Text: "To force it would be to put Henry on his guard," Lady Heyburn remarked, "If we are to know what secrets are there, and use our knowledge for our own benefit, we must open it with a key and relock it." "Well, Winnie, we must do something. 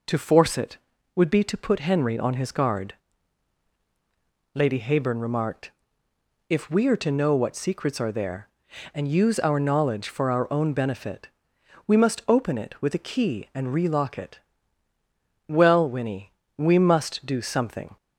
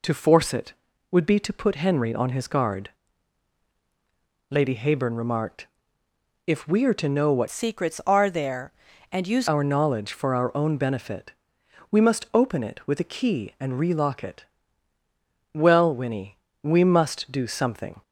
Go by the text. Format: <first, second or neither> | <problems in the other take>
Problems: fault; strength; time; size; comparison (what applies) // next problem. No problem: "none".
first | changes voice from "secrets" to "use"; from 7.4 to 9.4 s; 2.0 s long